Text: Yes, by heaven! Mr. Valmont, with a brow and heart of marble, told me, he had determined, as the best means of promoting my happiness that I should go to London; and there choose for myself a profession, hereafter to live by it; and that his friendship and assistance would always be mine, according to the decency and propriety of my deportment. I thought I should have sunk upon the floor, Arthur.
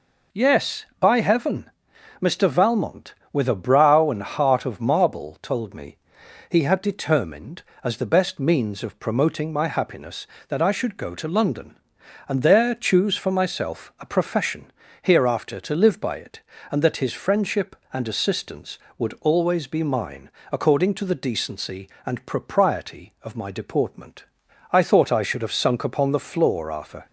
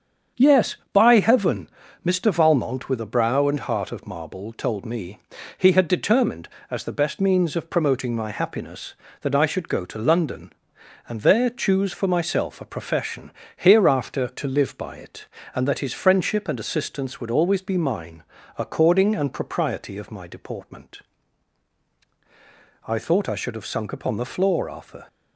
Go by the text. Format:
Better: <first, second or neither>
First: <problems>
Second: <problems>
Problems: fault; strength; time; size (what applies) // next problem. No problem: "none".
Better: first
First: none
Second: starts louder than the rest; strong; until 1.5 s; 7.5 dB // skips "to the decency"; at 19.1 s